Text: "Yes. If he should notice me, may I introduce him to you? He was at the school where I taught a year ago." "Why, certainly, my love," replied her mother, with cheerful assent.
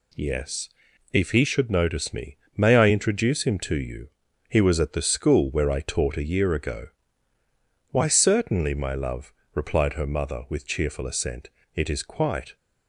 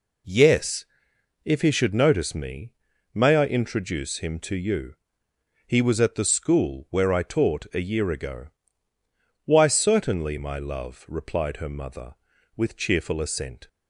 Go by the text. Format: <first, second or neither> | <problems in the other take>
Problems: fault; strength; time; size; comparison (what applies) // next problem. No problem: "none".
second | goes on to say "It is quite"; noticeable; from 11.7 s on; 0.80 s long